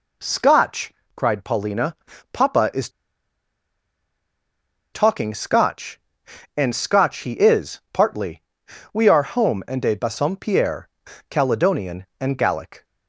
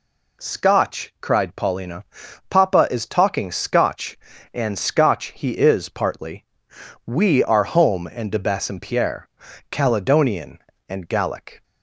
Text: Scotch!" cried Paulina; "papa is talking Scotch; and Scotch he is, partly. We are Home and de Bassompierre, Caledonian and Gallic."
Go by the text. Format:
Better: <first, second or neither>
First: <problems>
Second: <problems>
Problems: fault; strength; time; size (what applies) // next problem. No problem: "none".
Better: second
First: pauses between "is" and "talking"; strong; at 2.8 s; 2.0 s long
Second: none